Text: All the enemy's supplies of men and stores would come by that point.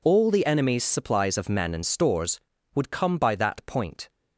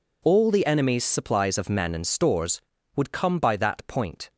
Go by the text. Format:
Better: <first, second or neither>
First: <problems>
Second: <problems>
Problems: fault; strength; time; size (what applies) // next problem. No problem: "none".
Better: neither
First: none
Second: none